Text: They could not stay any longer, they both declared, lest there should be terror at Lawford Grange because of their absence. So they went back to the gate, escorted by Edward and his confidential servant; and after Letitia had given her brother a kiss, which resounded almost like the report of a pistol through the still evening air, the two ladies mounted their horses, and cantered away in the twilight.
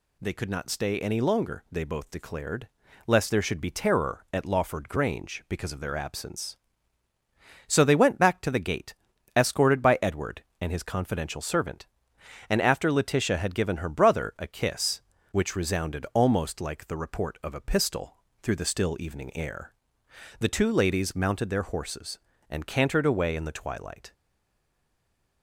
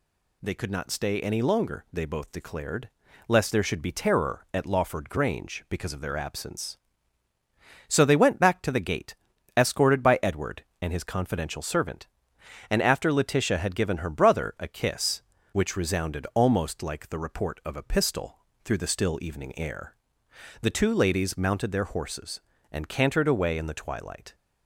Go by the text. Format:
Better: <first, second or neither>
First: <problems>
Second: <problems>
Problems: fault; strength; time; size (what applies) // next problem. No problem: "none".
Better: second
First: pauses between "pistol" and "through"; slight; at 18.1 s; 0.26 s long // stays silent after the last word; noticeable; from 24.1 s on; 1.3 s long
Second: pauses between "pistol" and "through"; slight; at 18.3 s; 0.26 s long